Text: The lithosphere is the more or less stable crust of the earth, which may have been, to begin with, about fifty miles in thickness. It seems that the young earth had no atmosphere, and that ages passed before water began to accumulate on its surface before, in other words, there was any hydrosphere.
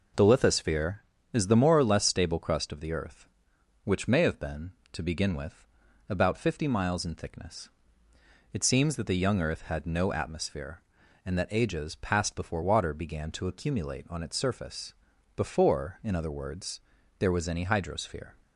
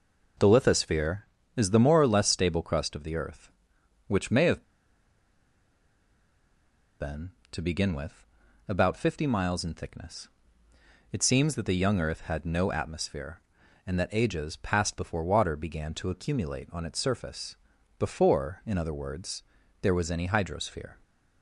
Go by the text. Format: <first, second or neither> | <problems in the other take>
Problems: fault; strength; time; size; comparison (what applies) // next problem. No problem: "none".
first | pauses between "have" and "been"; strong; at 4.6 s; 2.3 s long // pauses between "surface" and "before"; at 17.5 s; 0.44 s long; also in the first